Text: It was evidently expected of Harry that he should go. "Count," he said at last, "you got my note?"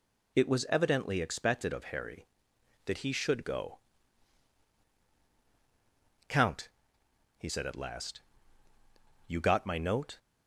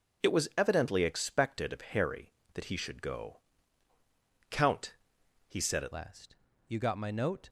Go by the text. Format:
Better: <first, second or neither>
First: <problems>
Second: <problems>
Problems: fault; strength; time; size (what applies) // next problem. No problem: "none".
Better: first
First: none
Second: changes voice at "last"; from 5.9 s on; 1.5 s long